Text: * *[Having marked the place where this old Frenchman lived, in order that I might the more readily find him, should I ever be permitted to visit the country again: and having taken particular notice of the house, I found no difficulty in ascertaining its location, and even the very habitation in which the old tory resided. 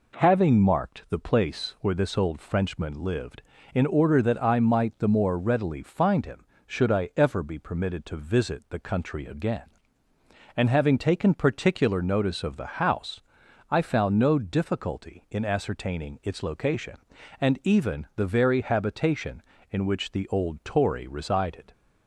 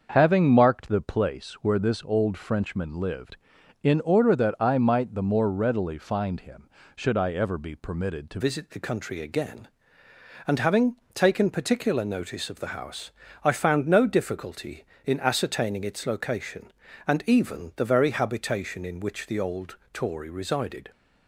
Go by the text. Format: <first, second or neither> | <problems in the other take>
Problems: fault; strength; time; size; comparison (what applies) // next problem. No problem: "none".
first | starts louder than the rest; until 1.1 s; 6.5 dB // changes voice at "visit"; from 8.4 s on; 12.5 s long // pauses between "having" and "taken"; slight; at 10.9 s; 0.18 s long // pauses between "old" and "tory"; slight; at 19.7 s; 0.16 s long